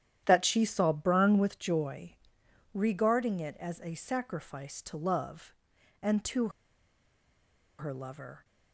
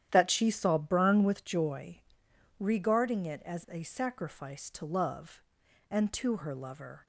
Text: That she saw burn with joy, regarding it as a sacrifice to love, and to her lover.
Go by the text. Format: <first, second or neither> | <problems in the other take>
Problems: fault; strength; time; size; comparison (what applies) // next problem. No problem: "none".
second | starts louder than the rest; strong; until 1.2 s; 10.5 dB; strong in the second // pauses between "to" and "her"; strong; at 6.4 s; 1.2 s long